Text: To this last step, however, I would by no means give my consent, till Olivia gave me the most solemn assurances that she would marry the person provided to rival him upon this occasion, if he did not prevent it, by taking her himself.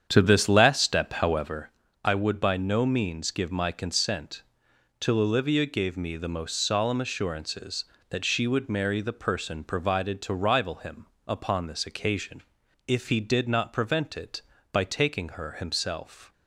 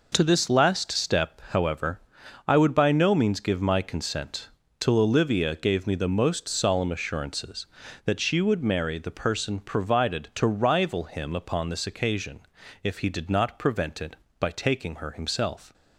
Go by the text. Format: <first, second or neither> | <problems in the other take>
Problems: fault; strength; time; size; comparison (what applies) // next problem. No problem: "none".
second | starts louder than the rest; strong; until 1.7 s; 8.5 dB // pauses between "him" and "upon"; slight; at 11.0 s; 0.18 s long